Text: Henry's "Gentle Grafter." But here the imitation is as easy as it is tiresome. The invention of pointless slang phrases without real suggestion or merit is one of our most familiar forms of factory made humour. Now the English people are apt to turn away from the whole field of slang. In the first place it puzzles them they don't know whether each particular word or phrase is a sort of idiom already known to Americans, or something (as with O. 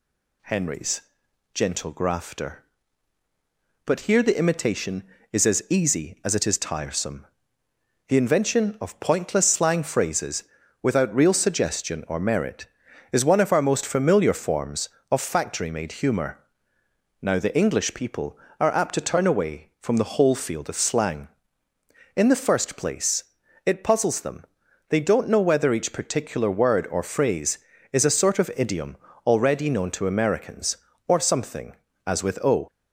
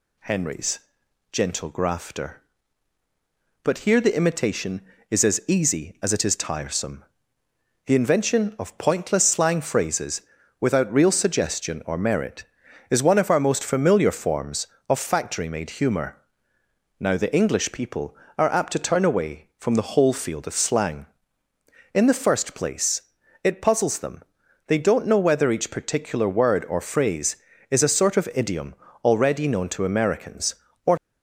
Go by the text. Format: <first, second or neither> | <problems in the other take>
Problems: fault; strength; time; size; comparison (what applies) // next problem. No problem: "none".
first | pauses between "Henry's" and "Gentle"; noticeable; at 0.7 s; 0.52 s long; noticeable in the first // pauses between "phrases" and "without"; at 10.2 s; 0.38 s long; also in the first // pauses between "place" and "it"; at 23.0 s; 0.42 s long; also in the first // pauses between "them" and "they"; at 24.2 s; 0.44 s long; also in the first // pauses between "idiom" and "already"; slight; at 28.7 s; 0.28 s long; slight in the first // stops before "something as with O"; at 30.9 s